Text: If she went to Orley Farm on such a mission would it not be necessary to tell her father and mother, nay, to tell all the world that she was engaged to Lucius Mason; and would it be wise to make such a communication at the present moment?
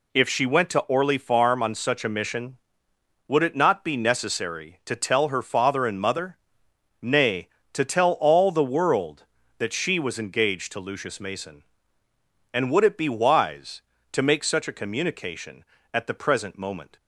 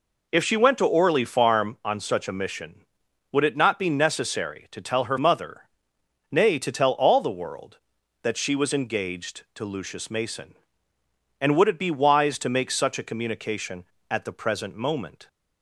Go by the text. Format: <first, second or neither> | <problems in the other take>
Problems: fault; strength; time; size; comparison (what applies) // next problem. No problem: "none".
first | skips "father and"; at 5.1 s